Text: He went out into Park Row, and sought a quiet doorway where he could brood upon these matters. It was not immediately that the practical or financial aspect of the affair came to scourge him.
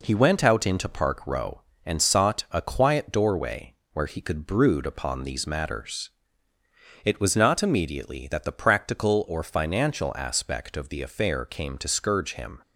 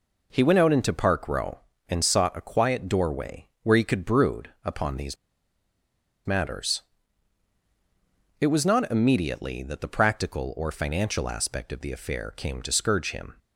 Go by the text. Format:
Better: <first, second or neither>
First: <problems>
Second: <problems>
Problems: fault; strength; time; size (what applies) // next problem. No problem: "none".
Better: first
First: pauses between "doorway" and "where"; slight; at 3.7 s; 0.20 s long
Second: pauses between "doorway" and "where"; slight; at 3.4 s; 0.16 s long // pauses between "these" and "matters"; at 5.1 s; 1.1 s long